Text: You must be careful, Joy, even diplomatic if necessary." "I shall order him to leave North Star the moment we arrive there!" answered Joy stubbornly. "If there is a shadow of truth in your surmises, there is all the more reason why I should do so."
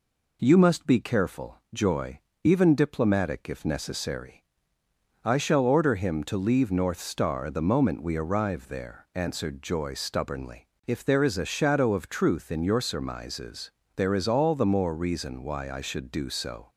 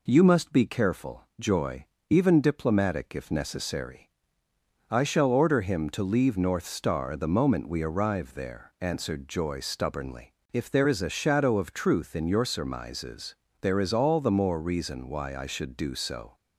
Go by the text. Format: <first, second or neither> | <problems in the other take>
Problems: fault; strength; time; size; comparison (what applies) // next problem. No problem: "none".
neither | none